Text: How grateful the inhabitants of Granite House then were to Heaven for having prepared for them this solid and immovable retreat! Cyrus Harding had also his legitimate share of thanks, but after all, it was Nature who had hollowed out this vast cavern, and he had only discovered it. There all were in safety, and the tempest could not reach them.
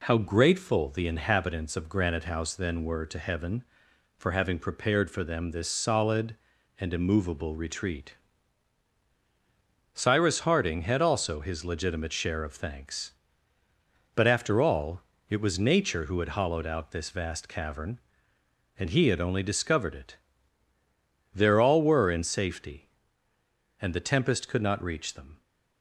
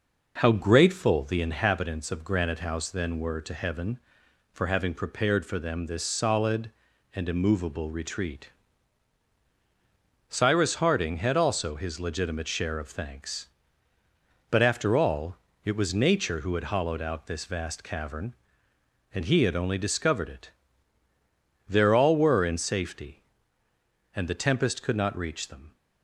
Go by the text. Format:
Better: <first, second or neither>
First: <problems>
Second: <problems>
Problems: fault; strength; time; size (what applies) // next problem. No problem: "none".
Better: first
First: none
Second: starts louder than the rest; noticeable; until 1.6 s; 5.5 dB